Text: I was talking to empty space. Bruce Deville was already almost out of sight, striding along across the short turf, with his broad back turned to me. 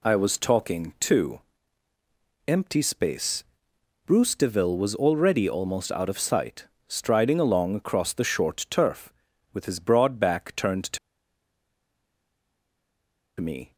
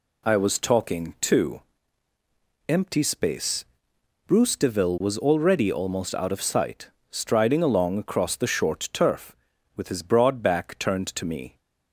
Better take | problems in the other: second | pauses between "to" and "empty"; at 1.3 s; 1.0 s long; also in the second // pauses between "to" and "me"; strong; at 10.9 s; 2.4 s long

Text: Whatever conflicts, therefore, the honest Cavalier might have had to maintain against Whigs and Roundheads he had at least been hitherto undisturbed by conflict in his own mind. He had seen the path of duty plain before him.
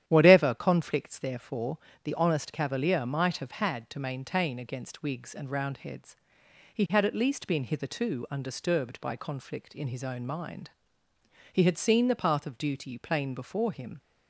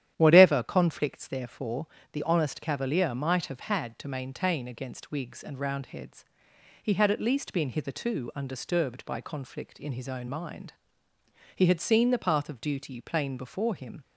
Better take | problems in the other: neither | starts louder than the rest; strong; the same in both // pauses between "Roundheads" and "he"; noticeable; the same in both

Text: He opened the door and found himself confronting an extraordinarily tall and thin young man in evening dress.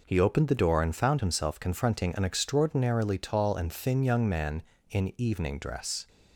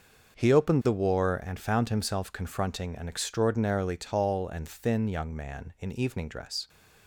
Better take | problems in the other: first | starts louder than the rest; until 1.5 s; 6.5 dB // says "war" for "door"; at 0.9 s

